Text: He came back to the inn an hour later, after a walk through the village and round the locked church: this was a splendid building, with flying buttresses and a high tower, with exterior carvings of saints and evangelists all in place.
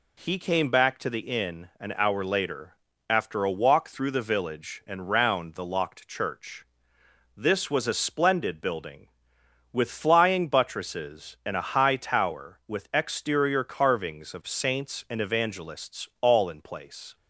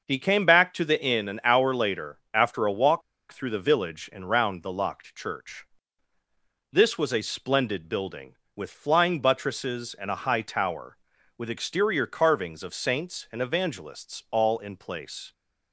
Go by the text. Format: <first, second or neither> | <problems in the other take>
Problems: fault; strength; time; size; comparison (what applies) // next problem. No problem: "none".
first | starts louder than the rest; noticeable; until 1.0 s; 6 dB // pauses between "walk" and "through"; slight; at 3.0 s; 0.30 s long